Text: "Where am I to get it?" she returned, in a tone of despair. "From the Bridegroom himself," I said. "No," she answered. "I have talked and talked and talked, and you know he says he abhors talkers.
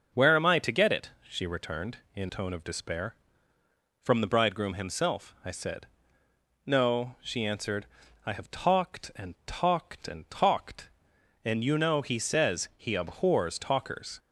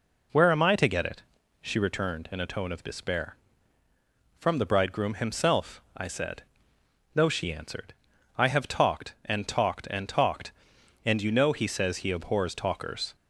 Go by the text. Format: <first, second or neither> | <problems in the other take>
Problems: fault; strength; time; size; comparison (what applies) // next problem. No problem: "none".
second | starts louder than the rest; noticeable; until 1.3 s; 6 dB // skips "a"; at 2.2 s